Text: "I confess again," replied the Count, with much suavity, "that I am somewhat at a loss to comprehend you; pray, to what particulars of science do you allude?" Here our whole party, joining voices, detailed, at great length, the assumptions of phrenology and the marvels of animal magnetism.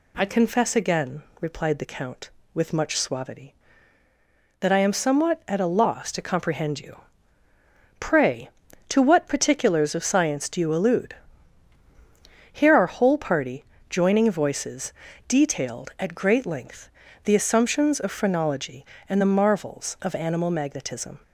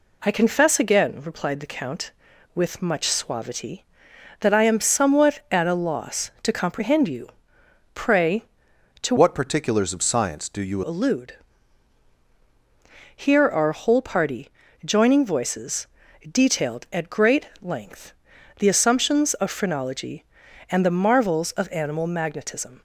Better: first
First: none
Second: changes voice from "what" to "you"; from 9.1 to 10.8 s; 1.7 s long

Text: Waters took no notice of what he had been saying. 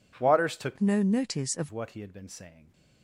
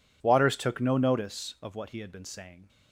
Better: second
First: changes voice from "no" to "of"; from 0.7 to 1.6 s; 0.9 s long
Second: none

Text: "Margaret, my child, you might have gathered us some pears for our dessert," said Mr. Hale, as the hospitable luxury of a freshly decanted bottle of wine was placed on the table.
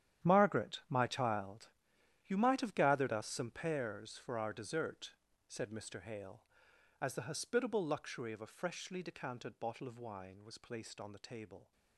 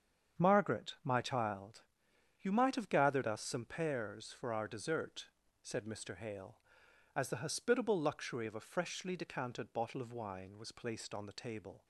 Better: second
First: gets quieter; strong; throughout; 15.5 dB // starts louder than the rest; strong; until 1.3 s; 10.5 dB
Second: starts louder than the rest; strong; until 1.4 s; 7.5 dB

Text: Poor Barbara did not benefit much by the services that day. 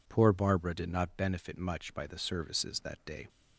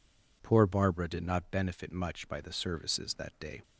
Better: neither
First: none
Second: none

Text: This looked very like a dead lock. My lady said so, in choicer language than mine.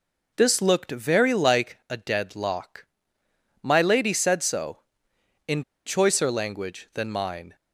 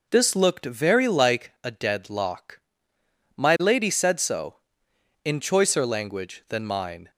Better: second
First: pauses between "in" and "choicer"; slight; at 5.6 s; 0.25 s long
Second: none

